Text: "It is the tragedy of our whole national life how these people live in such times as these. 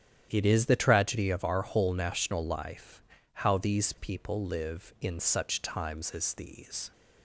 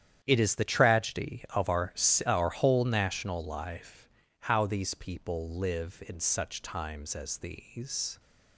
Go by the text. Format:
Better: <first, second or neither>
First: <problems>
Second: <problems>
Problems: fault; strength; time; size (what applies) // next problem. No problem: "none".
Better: first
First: starts louder than the rest; strong; until 1.3 s; 10 dB // pauses between "life" and "how"; slight; at 3.0 s; 0.30 s long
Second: starts louder than the rest; strong; until 1.2 s; 9.5 dB // says "our" twice; at 2.2 s // pauses between "life" and "how"; slight; at 4.0 s; 0.34 s long